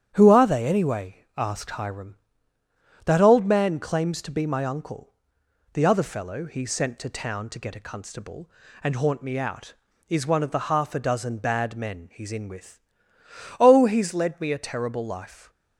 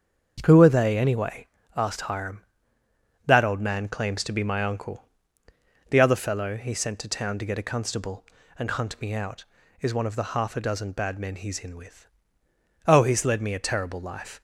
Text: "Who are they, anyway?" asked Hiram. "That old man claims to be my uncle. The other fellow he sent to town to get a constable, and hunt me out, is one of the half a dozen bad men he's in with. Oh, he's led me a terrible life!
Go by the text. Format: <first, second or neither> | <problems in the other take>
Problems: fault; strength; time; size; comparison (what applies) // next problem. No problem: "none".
second | starts louder than the rest; strong; until 1.1 s; 9.5 dB; also in the second // says "haunt" for "hunt"; at 8.9 s